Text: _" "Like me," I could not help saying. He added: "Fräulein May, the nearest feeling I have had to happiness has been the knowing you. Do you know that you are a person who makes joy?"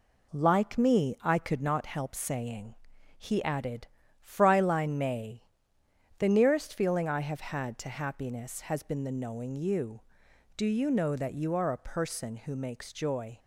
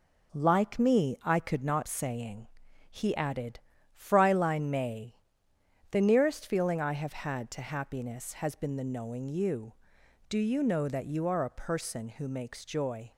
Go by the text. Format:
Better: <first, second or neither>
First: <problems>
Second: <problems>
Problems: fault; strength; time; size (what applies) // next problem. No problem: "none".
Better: first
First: none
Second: skips "help"; at 1.8 s